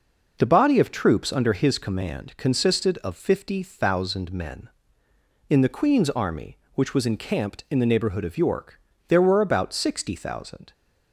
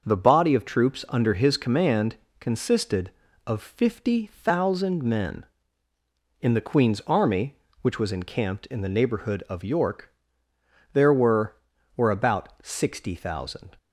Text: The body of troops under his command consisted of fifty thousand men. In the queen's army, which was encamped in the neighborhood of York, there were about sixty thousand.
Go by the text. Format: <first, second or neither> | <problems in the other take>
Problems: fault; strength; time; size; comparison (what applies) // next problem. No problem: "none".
first | starts louder than the rest; until 1.0 s; 6.5 dB // pauses between "command" and "consisted"; slight; at 2.1 s; 0.24 s long // says "were" twice; at 11.9 s